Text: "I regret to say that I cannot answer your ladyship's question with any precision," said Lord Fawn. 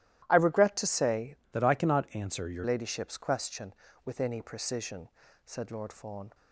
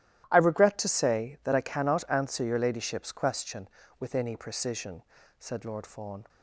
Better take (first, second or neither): second